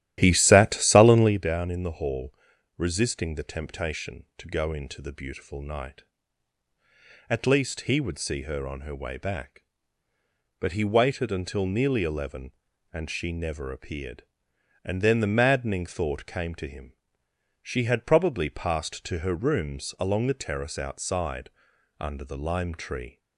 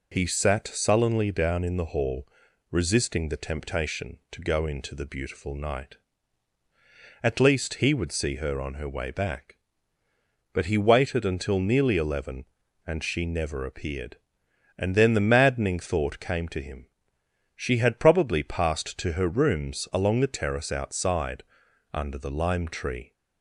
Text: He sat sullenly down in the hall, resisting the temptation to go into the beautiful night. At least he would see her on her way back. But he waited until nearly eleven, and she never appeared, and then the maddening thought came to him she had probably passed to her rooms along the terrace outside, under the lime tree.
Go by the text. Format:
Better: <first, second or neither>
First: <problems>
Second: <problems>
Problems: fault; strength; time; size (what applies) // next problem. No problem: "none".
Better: second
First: starts louder than the rest; strong; until 1.4 s; 13 dB // pauses between "him" and "she"; noticeable; at 16.9 s; 0.72 s long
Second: pauses between "him" and "she"; noticeable; at 16.8 s; 0.72 s long